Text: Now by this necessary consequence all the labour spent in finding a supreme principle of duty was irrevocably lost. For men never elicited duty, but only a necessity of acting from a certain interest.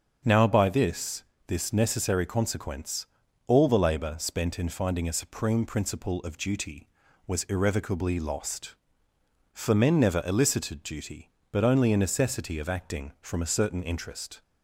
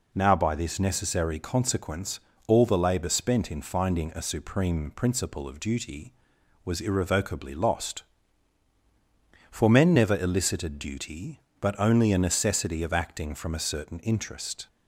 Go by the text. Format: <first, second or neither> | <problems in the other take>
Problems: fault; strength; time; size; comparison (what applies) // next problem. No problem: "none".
second | starts louder than the rest; until 1.5 s; 7 dB // says "this" twice; at 1.4 s // pauses between "consequence" and "all"; at 3.0 s; 0.40 s long; slight in the second